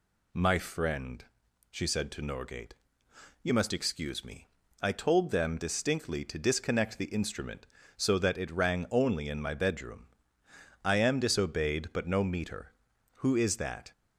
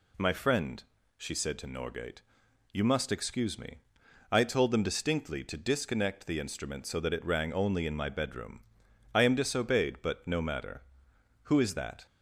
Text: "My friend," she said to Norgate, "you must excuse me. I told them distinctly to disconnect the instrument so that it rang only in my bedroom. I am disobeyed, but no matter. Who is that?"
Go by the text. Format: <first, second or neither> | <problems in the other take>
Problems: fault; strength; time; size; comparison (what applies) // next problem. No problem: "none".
second | says "meter" for "matter"; at 12.2 s